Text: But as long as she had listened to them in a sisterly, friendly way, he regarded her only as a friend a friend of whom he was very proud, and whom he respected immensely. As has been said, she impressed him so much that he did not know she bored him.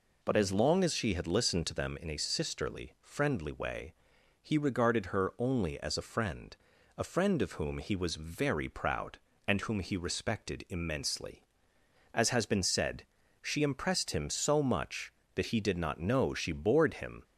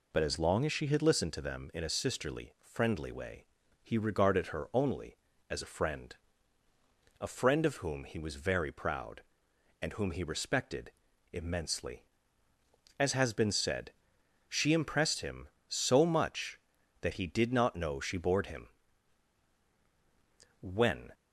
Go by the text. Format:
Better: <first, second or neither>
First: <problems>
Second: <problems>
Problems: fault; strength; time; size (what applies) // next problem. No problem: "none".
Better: first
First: pauses between "friend" and "a"; at 6.5 s; 0.42 s long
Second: pauses between "friend" and "a"; at 6.1 s; 1.0 s long // pauses between "respected" and "immensely"; at 10.9 s; 0.40 s long // goes on to say "When"; from 20.6 s on; 0.52 s long